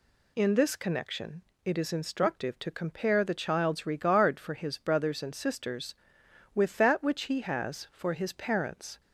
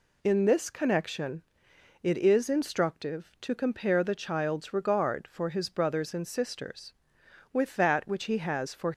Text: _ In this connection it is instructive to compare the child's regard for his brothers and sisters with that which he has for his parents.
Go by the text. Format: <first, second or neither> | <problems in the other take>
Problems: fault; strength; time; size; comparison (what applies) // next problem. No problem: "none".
first | pauses between "connection" and "it"; noticeable; at 1.4 s; 0.62 s long; slight in the first // stops before "his parents"; at 8.9 s